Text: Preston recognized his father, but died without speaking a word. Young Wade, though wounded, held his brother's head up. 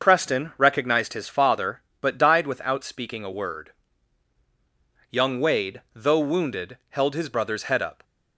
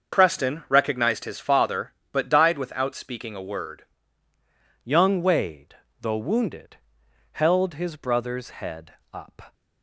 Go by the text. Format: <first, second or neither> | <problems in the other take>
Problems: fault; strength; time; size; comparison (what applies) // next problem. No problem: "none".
first | starts louder than the rest; until 1.2 s; 6.5 dB; also in the first // changes voice at "Young"; from 4.8 s on; 4.7 s long // pauses between "head" and "up"; slight; at 8.9 s; 0.20 s long